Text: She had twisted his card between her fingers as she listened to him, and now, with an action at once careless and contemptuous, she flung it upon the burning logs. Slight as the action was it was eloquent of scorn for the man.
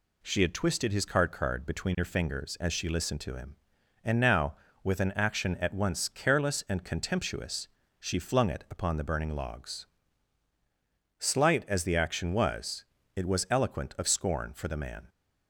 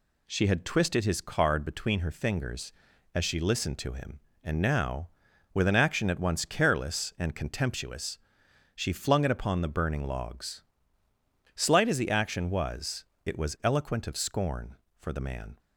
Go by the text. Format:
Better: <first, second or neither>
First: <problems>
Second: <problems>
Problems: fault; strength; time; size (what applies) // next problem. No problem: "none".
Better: second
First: says "card" twice; at 1.3 s // pauses between "was" and "it"; slight; at 12.8 s; 0.30 s long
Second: pauses between "was" and "it"; slight; at 13.0 s; 0.20 s long